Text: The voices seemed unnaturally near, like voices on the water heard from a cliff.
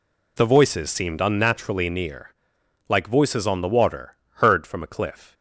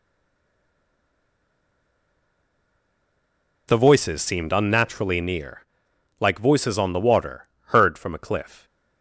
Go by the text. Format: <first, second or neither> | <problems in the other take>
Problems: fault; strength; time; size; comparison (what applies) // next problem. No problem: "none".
first | stays silent before the first word; strong; until 3.6 s; 3.6 s long // pauses between "water" and "heard"; slight; at 7.4 s; 0.20 s long; slight in the first